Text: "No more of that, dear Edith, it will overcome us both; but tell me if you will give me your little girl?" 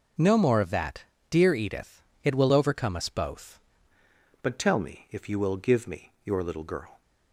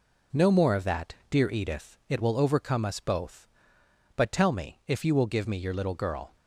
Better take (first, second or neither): second